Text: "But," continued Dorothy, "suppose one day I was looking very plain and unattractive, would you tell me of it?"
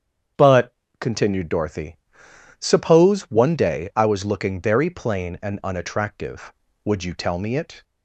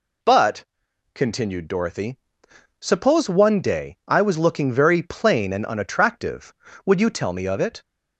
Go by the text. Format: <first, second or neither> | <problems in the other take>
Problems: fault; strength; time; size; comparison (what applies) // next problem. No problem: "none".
second | starts louder than the rest; strong; until 1.6 s; 8 dB // skips "of"; at 7.5 s